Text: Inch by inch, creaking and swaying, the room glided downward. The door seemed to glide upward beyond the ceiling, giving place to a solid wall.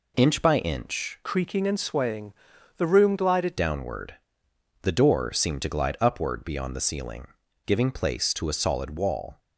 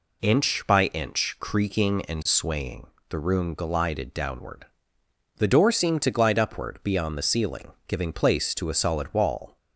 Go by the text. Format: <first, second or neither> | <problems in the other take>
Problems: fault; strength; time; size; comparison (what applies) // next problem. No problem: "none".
second | changes voice from "creaking" to "glided"; from 1.2 to 3.5 s; 2.3 s long